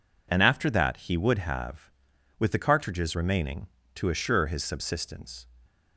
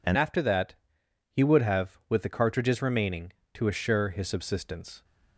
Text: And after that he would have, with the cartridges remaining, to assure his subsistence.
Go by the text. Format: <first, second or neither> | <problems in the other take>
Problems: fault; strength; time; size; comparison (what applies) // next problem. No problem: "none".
first | changes voice at "after"; from 0.1 s on; 4.9 s long // pauses between "that" and "he"; noticeable; at 0.7 s; 0.58 s long